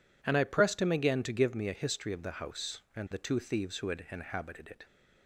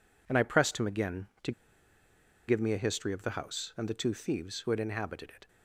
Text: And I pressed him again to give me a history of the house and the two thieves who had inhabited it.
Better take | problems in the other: first | pauses between "to" and "give"; noticeable; at 1.5 s; 0.96 s long

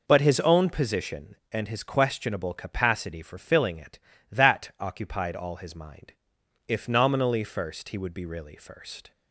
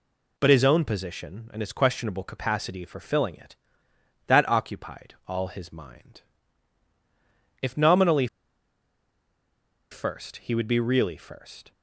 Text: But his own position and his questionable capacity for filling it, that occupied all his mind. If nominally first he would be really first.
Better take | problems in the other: first | pauses between "nominally" and "first"; strong; at 8.2 s; 1.6 s long

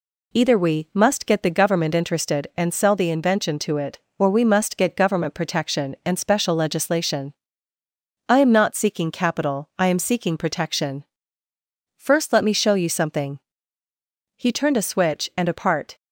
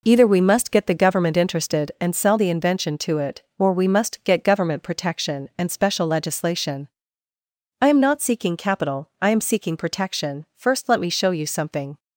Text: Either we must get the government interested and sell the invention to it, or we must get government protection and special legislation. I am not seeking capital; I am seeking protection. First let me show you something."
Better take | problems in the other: second | goes on to say "He turned a switch and a part"; from 14.3 s on; 1.6 s long

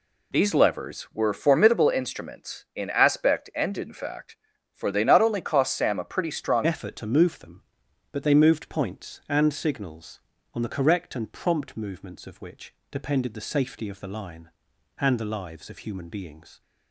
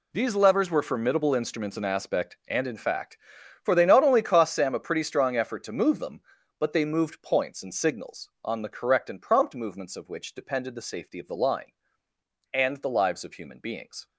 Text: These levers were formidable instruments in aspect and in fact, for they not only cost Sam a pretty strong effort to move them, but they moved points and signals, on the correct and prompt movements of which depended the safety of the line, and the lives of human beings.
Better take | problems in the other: second | changes voice at "effort"; from 6.6 s on; 10.0 s long // pauses between "which" and "depended"; slight; at 12.7 s; 0.18 s long

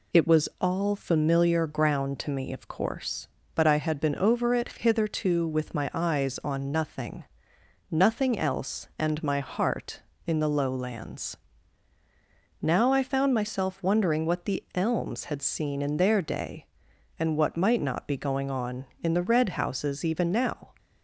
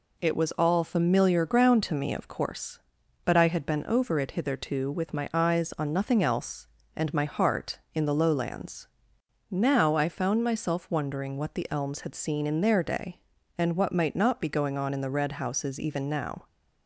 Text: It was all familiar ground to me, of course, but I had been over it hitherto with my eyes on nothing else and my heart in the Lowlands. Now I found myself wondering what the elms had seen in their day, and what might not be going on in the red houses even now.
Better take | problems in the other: second | says "nothing" twice; at 7.8 s

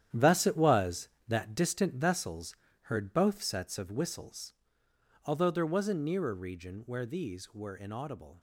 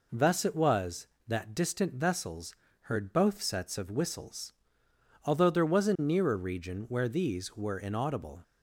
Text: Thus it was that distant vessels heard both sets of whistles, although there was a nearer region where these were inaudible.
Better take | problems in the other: second | gets quieter; strong; throughout; 10.5 dB // pauses between "vessels" and "heard"; slight; at 2.5 s; 0.26 s long; slight in the second

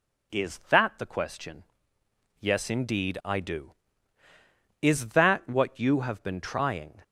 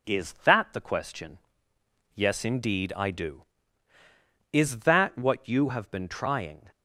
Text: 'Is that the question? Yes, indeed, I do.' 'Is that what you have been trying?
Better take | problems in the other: first | gets quieter; slight; throughout; 2.5 dB

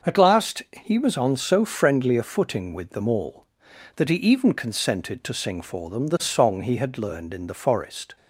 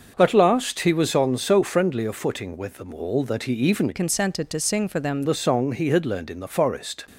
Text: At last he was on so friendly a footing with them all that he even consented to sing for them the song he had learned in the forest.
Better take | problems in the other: first | starts louder than the rest; until 1.1 s; 6 dB; noticeable in the first // changes voice from "consented" to "them"; from 3.9 to 5.2 s; 1.3 s long

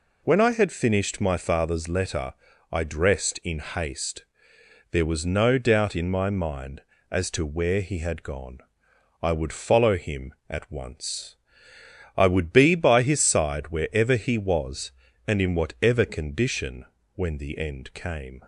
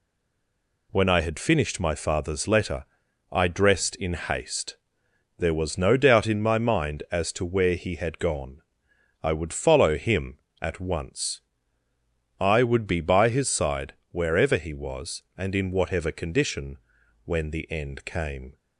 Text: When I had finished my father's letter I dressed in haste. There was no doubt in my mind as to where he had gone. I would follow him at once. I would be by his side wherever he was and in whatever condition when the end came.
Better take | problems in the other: first | stays silent before the first word; slight; until 0.9 s; 0.9 s long // pauses between "letter" and "I"; noticeable; at 2.8 s; 0.46 s long; also in the first // pauses between "side" and "wherever"; slight; at 13.9 s; 0.18 s long // pauses between "condition" and "when"; noticeable; at 16.7 s; 0.48 s long; slight in the first

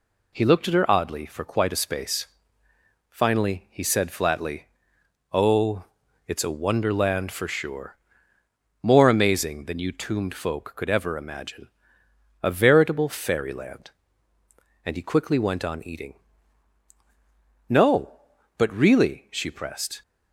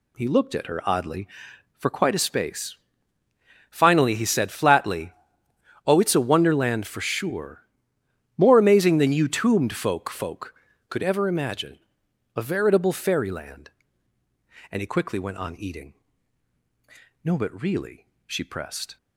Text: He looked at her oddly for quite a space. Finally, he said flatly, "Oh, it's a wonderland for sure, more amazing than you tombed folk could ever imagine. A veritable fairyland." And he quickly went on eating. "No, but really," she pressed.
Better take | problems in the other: first | says "folk" twice; at 10.0 s

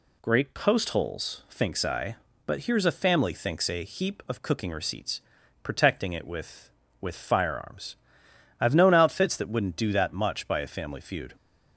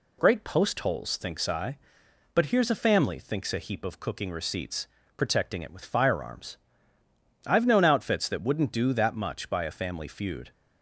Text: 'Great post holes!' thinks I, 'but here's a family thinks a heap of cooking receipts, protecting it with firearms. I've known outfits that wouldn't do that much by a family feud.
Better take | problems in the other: second | says "with" twice; at 6.9 s

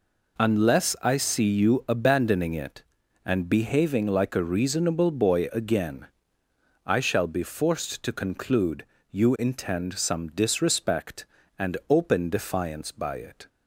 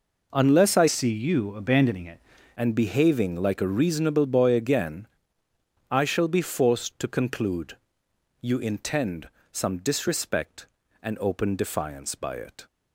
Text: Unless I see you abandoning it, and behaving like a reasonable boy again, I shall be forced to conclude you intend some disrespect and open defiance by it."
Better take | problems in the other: first | changes voice from "see" to "it"; from 0.8 to 2.2 s; 1.4 s long // pauses between "conclude" and "you"; noticeable; at 7.7 s; 0.64 s long; slight in the first // pauses between "intend" and "some"; slight; at 9.2 s; 0.22 s long

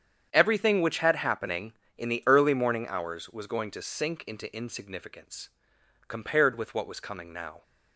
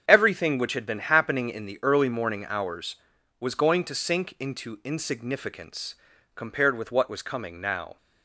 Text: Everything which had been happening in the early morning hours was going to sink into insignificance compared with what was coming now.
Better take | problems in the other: second | starts louder than the rest; strong; until 1.3 s; 8.5 dB; strong in the second // skips "been"; at 1.1 s // pauses between "insignificance" and "compared"; noticeable; at 5.4 s; 0.58 s long; also in the second

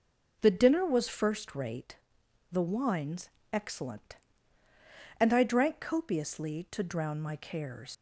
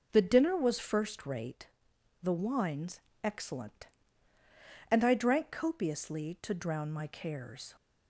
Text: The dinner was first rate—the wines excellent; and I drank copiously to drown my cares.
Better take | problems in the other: second | pauses between "wines" and "excellent"; slight; at 3.2 s; 0.24 s long; slight in the second // leaves "cares" unfinished; at 7.9 s; 95 ms

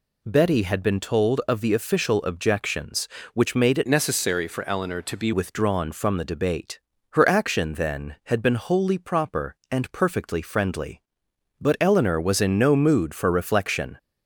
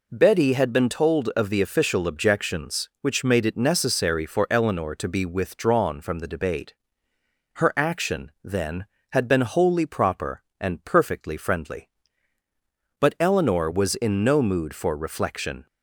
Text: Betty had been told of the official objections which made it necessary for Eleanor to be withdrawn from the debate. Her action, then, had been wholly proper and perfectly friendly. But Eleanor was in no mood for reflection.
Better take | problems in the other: second | changes voice from "necessary" to "be"; from 3.8 to 5.3 s; 1.5 s long

